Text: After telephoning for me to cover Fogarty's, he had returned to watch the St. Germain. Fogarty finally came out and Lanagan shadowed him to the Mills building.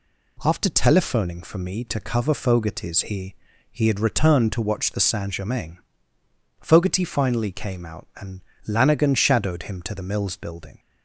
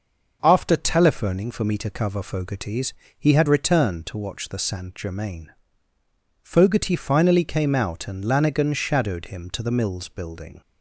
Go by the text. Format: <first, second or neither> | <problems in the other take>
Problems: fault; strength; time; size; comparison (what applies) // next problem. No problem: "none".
second | says "he" twice; at 3.7 s // pauses between "and" and "Lanagan"; slight; at 8.3 s; 0.28 s long